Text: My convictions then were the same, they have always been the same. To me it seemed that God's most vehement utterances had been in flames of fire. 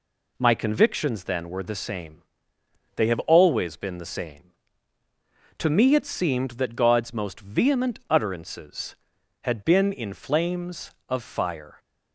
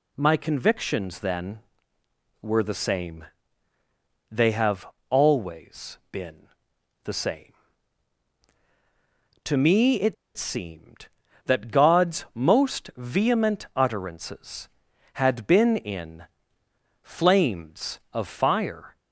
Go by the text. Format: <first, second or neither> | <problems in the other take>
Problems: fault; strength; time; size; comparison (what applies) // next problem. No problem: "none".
first | pauses between "have" and "always"; slight; at 4.8 s; 0.24 s long // pauses between "been" and "the"; noticeable; at 6.4 s; 0.56 s long // pauses between "it" and "seemed"; slight; at 10.1 s; 0.22 s long // pauses between "in" and "flames"; noticeable; at 16.2 s; 0.78 s long